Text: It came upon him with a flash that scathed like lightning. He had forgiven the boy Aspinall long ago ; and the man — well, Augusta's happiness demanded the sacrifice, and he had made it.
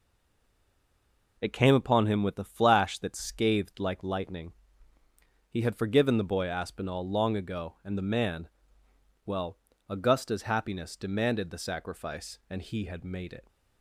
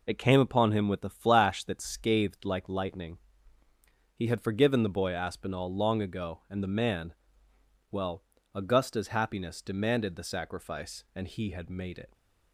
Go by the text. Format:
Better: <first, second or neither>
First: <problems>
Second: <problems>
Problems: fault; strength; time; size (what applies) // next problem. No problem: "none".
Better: second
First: stays silent before the first word; noticeable; until 1.3 s; 1.3 s long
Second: none